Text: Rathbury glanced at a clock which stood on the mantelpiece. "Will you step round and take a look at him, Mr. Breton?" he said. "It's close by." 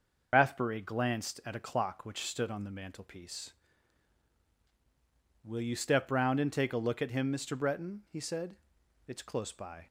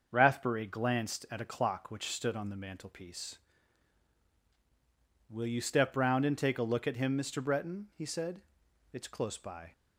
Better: second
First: loses the start of "Rathbury"; at 0.3 s; 80 ms // starts louder than the rest; noticeable; until 1.3 s; 6 dB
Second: starts louder than the rest; until 1.1 s; 6 dB

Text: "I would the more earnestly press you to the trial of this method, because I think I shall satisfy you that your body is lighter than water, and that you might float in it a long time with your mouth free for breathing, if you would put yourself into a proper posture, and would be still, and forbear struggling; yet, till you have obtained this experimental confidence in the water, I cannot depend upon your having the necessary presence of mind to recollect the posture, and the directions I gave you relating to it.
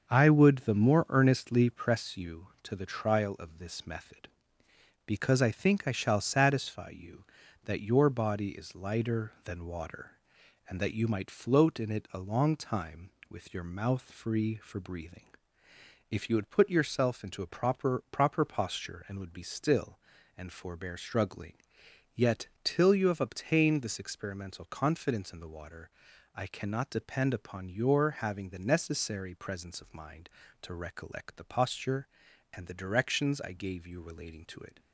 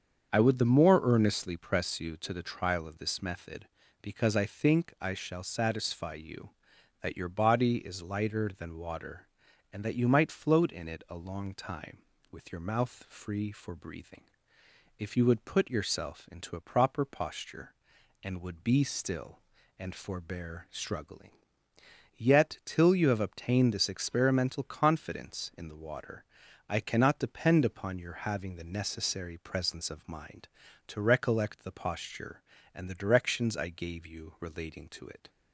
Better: second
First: starts louder than the rest; until 1.1 s; 6.5 dB // says "proper" twice; at 18.0 s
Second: starts louder than the rest; strong; until 1.3 s; 7 dB

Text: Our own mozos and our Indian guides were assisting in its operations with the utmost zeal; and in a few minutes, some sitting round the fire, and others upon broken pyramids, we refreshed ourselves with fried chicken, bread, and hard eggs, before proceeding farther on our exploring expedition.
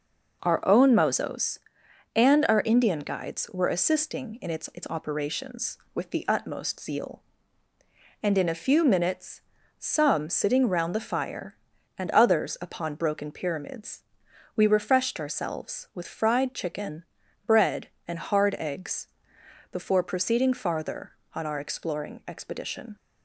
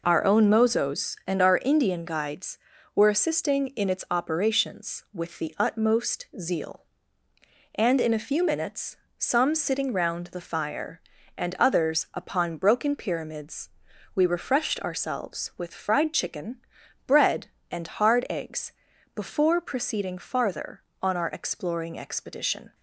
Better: second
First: says "its" twice; at 4.7 s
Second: none

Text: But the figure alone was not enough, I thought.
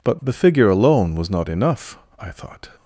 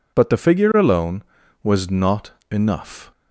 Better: first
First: none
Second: pauses between "not" and "enough"; slight; at 2.3 s; 0.20 s long // stops before "I thought"; at 3.1 s

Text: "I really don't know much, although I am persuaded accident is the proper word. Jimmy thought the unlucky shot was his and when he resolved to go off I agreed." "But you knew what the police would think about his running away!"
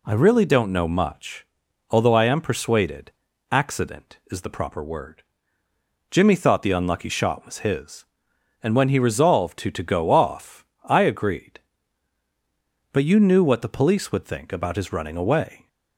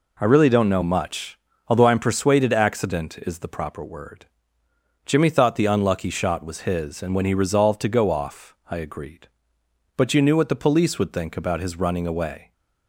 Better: second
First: pauses between "persuaded" and "accident"; at 3.1 s; 0.40 s long // says "to" twice; at 9.7 s // pauses between "off" and "I"; slight; at 10.6 s; 0.18 s long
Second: pauses between "off" and "I"; slight; at 8.5 s; 0.16 s long

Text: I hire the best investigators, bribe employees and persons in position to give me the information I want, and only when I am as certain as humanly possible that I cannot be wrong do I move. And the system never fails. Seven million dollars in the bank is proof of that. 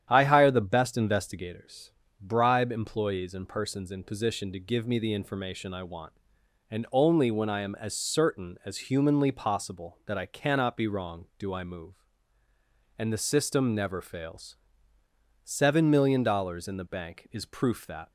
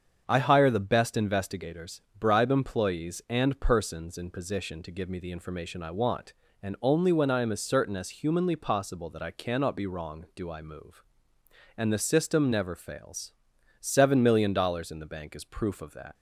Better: second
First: starts louder than the rest; strong; until 1.1 s; 9.5 dB // skips "of"; at 17.8 s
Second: starts louder than the rest; strong; until 1.2 s; 7 dB

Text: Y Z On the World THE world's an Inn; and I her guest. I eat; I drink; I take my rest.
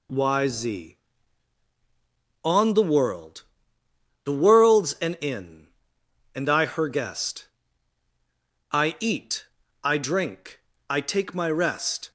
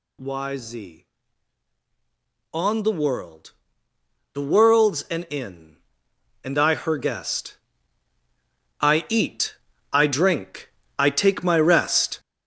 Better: first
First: pauses between "World" and "THE"; noticeable; at 3.4 s; 0.80 s long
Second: gets louder; strong; throughout; 8.5 dB // pauses between "World" and "THE"; noticeable; at 3.5 s; 0.80 s long

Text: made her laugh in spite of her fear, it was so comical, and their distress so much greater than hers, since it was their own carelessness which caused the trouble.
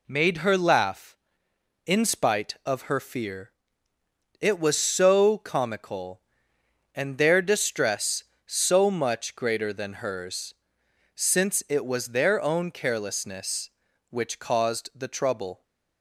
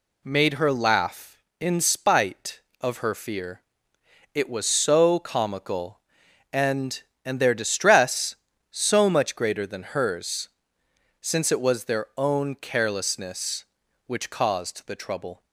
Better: first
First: none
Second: says "and" twice; at 7.2 s

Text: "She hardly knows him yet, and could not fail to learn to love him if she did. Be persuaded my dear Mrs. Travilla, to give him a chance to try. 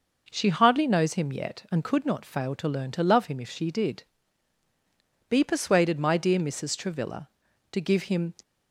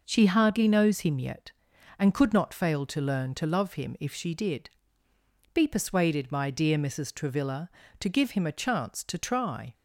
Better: second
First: stops before "a chance to try"; at 8.4 s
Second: none

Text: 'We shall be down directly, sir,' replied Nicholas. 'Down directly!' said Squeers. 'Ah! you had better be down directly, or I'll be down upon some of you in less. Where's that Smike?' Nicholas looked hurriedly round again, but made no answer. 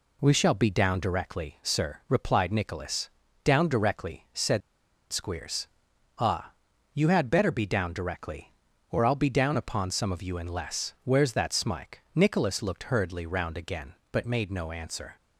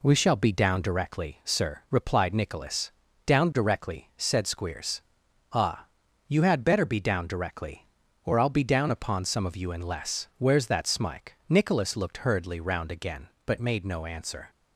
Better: second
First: pauses between "said" and "Squeers"; noticeable; at 4.6 s; 0.51 s long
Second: none

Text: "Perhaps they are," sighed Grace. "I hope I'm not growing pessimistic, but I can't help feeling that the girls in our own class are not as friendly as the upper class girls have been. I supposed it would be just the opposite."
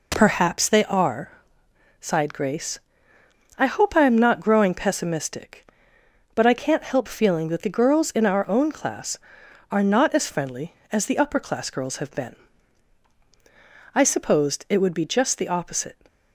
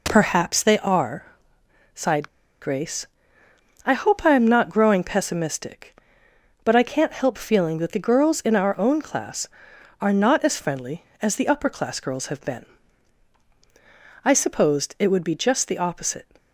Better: first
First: none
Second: pauses between "sighed" and "Grace"; slight; at 2.2 s; 0.33 s long

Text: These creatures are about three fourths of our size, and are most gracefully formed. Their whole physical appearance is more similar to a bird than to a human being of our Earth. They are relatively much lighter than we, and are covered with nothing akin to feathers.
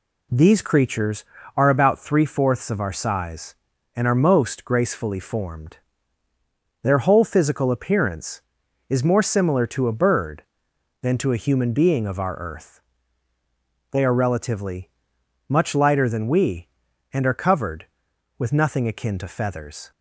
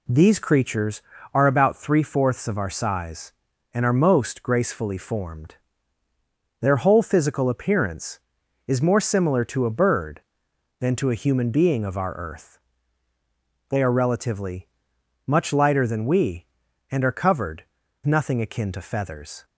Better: first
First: pauses between "relatively" and "much"; noticeable; at 14.9 s; 0.58 s long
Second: pauses between "relatively" and "much"; noticeable; at 14.6 s; 0.58 s long // skips "with"; at 17.8 s

